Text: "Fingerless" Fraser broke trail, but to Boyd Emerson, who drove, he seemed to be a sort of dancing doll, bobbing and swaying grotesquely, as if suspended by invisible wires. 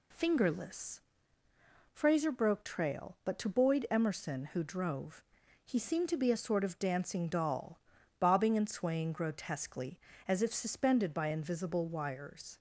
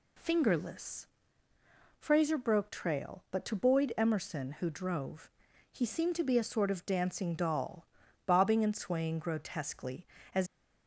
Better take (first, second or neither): first